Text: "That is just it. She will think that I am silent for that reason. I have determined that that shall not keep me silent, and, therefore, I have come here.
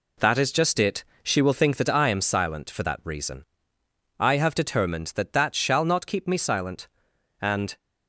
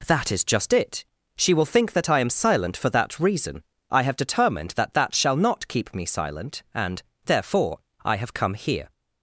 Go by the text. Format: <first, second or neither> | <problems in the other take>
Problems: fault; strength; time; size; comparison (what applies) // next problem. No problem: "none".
second | stops before "therefore I have come here"; at 7.7 s